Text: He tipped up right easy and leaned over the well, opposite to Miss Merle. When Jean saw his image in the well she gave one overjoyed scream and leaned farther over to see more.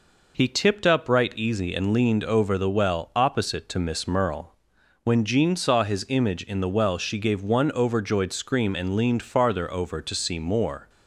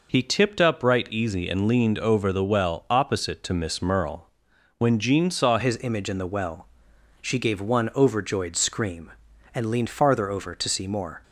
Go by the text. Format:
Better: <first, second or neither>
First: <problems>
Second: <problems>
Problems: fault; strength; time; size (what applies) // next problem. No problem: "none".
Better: first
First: none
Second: changes voice at "his"; from 5.5 s on; 5.7 s long // pauses between "well" and "she"; noticeable; at 6.6 s; 0.56 s long